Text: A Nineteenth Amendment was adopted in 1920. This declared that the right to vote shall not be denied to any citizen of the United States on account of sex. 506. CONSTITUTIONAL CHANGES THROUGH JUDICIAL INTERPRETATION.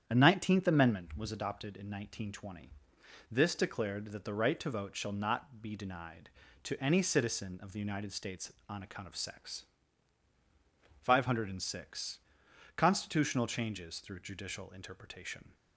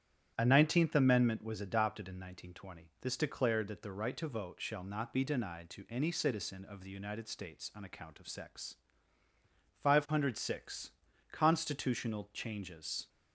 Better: first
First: starts louder than the rest; strong; until 1.0 s; 9 dB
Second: starts louder than the rest; strong; until 1.3 s; 10 dB // stops before "THROUGH JUDICIAL INTERPRETATION"; at 13.0 s

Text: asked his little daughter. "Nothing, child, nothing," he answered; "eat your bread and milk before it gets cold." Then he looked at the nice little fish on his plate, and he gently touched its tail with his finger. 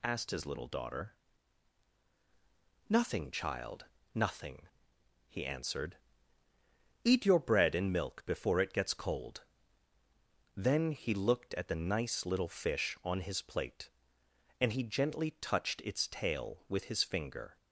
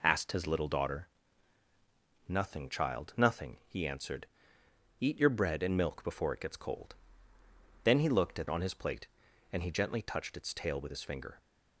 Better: first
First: none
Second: skips "the nice little fish"; at 8.4 s

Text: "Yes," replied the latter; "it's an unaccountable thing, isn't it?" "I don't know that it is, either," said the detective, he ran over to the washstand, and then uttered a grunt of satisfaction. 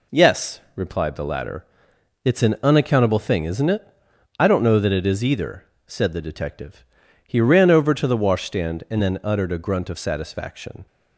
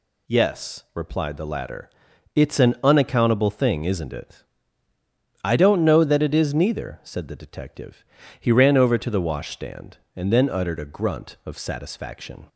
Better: first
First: none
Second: says "neither" for "either"; at 6.5 s

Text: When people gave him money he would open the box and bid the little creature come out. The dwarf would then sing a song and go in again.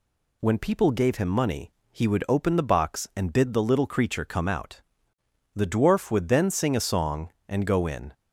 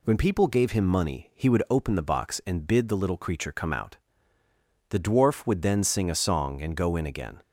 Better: second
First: pauses between "money" and "he"; slight; at 1.7 s; 0.20 s long // stops before "again"; at 8.1 s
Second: none

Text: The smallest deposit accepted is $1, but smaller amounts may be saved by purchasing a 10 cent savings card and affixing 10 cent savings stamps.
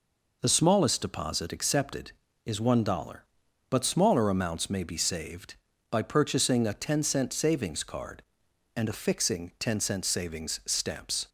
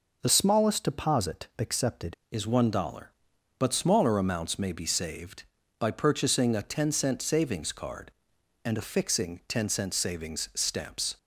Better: first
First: none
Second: changes voice from "smallest" to "accepted"; from 0.2 to 2.1 s; 1.9 s long

